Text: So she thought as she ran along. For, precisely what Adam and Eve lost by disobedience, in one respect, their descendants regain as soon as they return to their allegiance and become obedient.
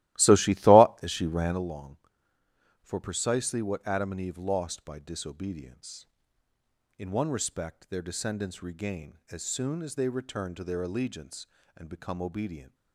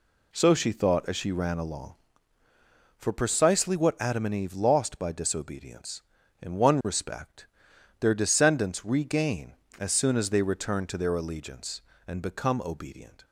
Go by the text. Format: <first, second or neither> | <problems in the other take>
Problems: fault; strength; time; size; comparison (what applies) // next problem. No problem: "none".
second | starts louder than the rest; strong; until 1.6 s; 16 dB